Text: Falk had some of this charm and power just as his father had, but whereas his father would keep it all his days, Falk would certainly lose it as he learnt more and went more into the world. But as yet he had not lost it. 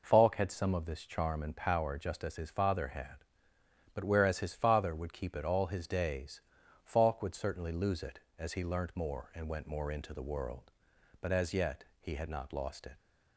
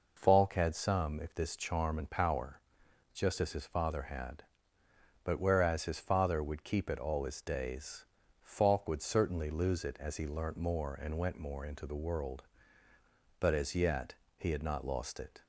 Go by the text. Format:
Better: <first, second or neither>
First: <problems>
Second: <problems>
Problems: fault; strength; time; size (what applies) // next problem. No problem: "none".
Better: first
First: pauses between "yet" and "he"; slight; at 11.8 s; 0.18 s long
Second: says "if" for "of"; at 1.1 s // pauses between "power" and "just"; noticeable; at 2.5 s; 0.54 s long // pauses between "yet" and "he"; slight; at 14.1 s; 0.24 s long